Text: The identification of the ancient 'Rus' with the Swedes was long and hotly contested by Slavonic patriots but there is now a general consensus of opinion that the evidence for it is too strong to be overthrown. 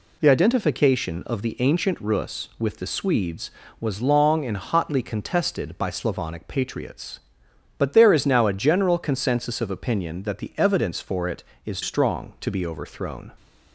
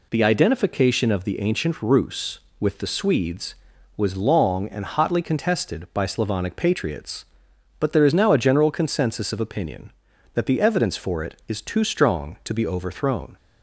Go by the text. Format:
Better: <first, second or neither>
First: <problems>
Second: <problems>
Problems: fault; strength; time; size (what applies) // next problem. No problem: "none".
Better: second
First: skips "too"; at 11.8 s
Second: none